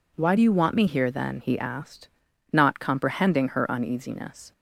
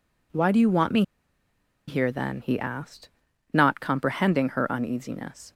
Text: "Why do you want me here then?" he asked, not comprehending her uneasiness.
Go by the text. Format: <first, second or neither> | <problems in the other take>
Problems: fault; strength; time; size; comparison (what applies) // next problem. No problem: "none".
first | pauses between "me" and "here"; noticeable; at 1.0 s; 0.85 s long